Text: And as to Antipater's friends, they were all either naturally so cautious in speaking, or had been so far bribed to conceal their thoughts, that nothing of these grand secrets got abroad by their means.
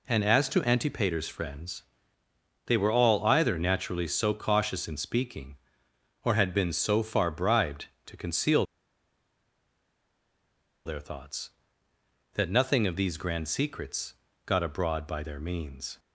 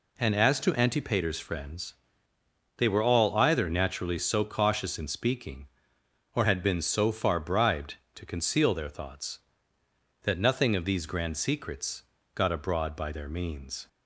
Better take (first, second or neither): second